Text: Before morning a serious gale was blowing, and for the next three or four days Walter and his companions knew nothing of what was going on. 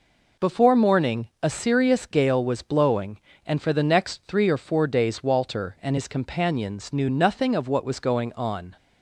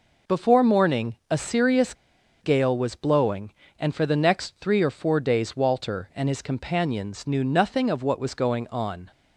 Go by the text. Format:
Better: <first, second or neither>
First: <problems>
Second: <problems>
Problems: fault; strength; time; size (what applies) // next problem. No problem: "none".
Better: first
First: none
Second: pauses between "serious" and "gale"; noticeable; at 1.9 s; 0.47 s long